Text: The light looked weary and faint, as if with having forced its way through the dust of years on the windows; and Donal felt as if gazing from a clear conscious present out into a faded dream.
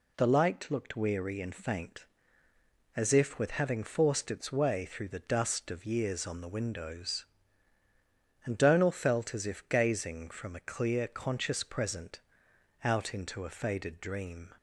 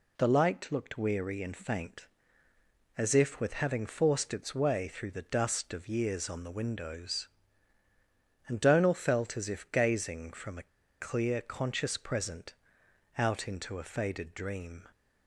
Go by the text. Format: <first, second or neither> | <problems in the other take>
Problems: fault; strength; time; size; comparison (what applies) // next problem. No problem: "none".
first | pauses between "a" and "clear"; slight; at 10.6 s; 0.31 s long // pauses between "present" and "out"; noticeable; at 12.5 s; 0.64 s long; noticeable in the first